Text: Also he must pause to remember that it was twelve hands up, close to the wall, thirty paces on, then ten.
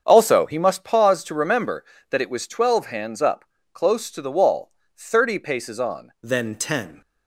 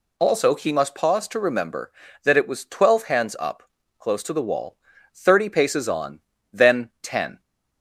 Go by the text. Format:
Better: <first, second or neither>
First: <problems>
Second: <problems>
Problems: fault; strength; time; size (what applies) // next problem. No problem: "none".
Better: second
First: starts louder than the rest; strong; until 1.0 s; 7.5 dB // changes voice at "then"; from 6.2 s on; 0.8 s long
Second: none